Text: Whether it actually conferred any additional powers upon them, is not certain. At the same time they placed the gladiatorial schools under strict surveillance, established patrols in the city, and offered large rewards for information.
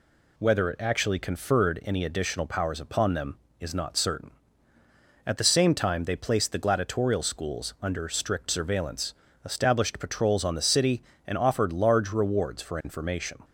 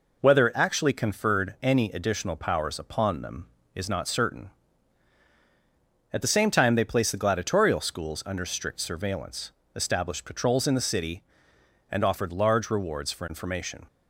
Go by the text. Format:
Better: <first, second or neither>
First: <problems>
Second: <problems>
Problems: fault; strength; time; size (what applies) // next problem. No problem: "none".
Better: second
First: says "on" for "in"; at 10.4 s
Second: none